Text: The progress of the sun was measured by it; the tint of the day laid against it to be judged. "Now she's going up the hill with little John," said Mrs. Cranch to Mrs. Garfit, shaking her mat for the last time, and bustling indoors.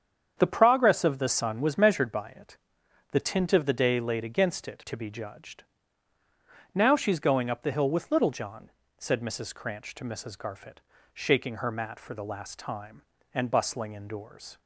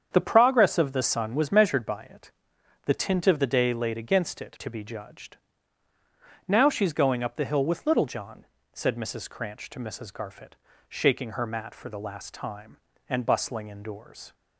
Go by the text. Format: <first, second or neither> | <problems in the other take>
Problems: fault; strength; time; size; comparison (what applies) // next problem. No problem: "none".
neither | starts louder than the rest; strong; the same in both